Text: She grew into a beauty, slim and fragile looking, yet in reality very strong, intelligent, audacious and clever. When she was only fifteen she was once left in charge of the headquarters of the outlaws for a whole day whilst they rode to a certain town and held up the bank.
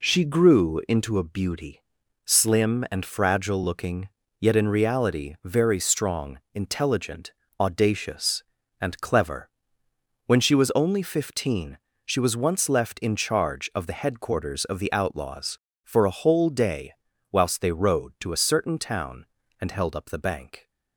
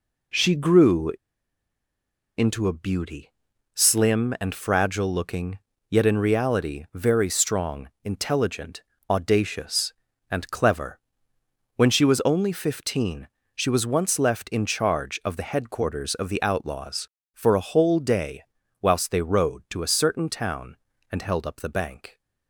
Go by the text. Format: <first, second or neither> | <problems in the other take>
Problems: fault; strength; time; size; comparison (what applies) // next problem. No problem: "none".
first | pauses between "grew" and "into"; at 1.1 s; 1.2 s long // pauses between "fifteen" and "she"; slight; at 13.2 s; 0.26 s long; slight in the first // pauses between "day" and "whilst"; at 18.4 s; 0.38 s long; also in the first